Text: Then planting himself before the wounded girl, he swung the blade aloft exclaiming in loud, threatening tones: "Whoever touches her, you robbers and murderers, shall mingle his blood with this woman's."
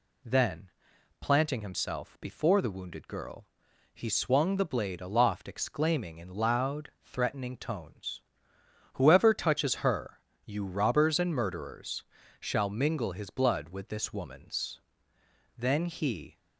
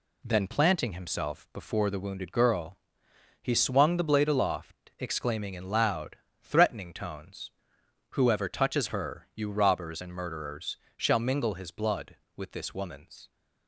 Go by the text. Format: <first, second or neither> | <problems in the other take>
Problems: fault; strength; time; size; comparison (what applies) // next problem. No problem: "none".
second | pauses between "Then" and "planting"; noticeable; at 0.6 s; 0.52 s long // goes on to say "Then he"; noticeable; from 15.5 s on; 0.82 s long